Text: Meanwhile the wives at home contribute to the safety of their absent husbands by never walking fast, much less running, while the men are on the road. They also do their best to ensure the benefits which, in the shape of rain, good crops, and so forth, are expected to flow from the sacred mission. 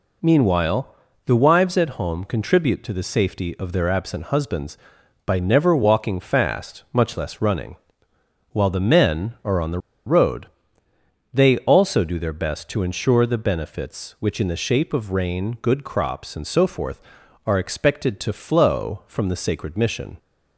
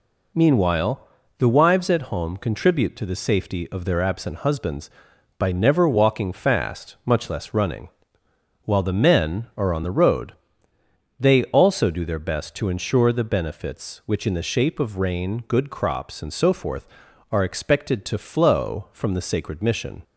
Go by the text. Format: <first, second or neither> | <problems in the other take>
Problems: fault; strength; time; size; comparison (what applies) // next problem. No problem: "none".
second | pauses between "Meanwhile" and "the"; slight; at 0.9 s; 0.32 s long; slight in the second // pauses between "the" and "road"; slight; at 9.7 s; 0.28 s long